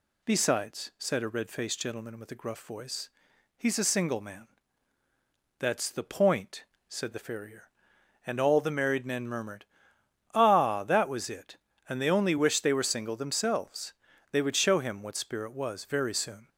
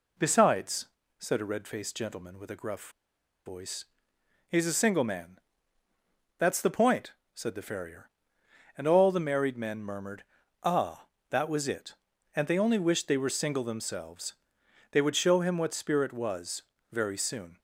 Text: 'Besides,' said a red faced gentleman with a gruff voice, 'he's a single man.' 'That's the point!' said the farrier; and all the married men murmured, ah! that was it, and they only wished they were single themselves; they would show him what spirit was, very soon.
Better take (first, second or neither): first